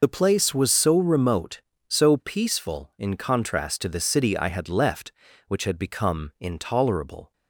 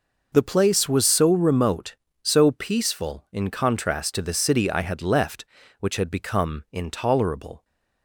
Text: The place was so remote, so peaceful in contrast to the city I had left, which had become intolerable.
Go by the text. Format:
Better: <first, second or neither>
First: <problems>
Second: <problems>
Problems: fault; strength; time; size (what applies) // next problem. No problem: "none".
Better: second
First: loses the start of "The"; at 0.0 s; 30 ms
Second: none